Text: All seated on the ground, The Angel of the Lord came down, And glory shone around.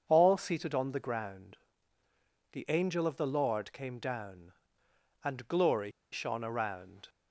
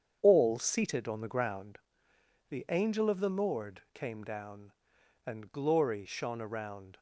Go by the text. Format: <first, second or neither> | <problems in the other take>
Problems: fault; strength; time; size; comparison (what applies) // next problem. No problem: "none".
second | starts louder than the rest; until 1.0 s; 6.5 dB; strong in the second // pauses between "glory" and "shone"; slight; at 5.9 s; 0.21 s long